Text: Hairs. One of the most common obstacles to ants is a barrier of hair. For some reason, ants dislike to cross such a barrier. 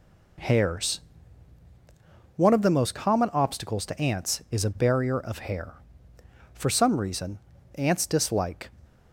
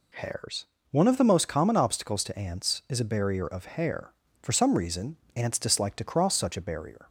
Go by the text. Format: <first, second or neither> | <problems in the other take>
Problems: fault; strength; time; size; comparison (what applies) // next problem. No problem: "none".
second | stops before "to cross such a barrier"; at 8.8 s